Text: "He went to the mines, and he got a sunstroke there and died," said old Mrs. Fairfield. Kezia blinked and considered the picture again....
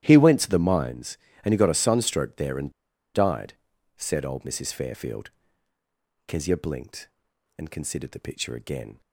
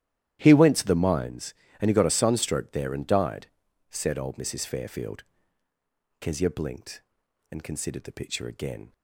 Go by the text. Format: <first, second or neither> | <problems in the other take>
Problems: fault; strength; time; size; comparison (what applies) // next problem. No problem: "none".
second | starts louder than the rest; strong; until 1.0 s; 12.5 dB; strong in the second // pauses between "and" and "died"; at 2.6 s; 0.44 s long